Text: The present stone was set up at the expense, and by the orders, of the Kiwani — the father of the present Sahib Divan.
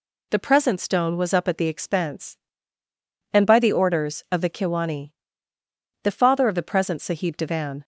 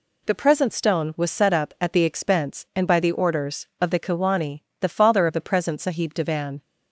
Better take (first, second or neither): second